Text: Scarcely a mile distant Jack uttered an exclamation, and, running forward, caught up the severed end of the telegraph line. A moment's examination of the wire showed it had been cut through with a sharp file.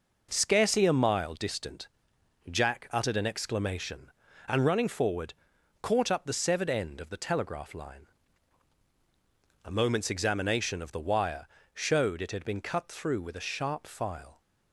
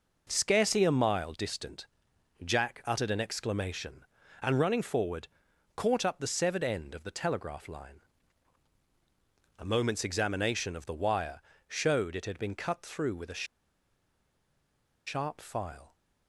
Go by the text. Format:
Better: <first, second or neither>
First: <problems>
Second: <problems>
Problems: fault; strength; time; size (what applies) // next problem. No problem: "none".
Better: first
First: pauses between "distant" and "Jack"; noticeable; at 1.8 s; 0.62 s long // pauses between "wire" and "showed"; slight; at 11.4 s; 0.26 s long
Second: pauses between "distant" and "Jack"; noticeable; at 1.8 s; 0.58 s long // pauses between "wire" and "showed"; slight; at 11.3 s; 0.26 s long // pauses between "a" and "sharp"; strong; at 13.4 s; 1.6 s long